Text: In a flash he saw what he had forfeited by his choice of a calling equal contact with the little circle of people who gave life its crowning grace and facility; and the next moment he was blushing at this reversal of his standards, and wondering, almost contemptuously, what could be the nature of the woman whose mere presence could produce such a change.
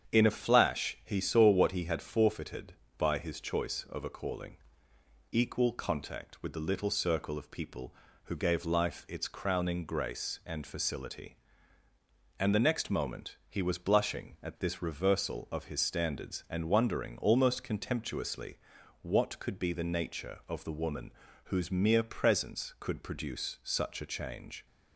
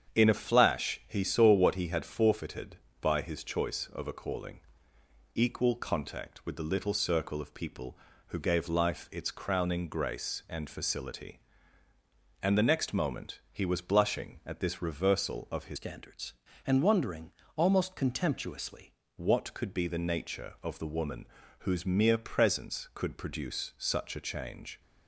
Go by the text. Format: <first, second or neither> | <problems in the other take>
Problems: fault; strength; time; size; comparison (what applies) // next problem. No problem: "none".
first | starts louder than the rest; strong; until 1.2 s; 7.5 dB; strong in the first // pauses between "calling" and "equal"; noticeable; at 4.5 s; 0.76 s long; noticeable in the first // changes voice from "standards" to "contemptuously"; from 15.7 to 18.9 s; 3.2 s long // pauses between "woman" and "whose"; slight; at 21.2 s; 0.32 s long; slight in the first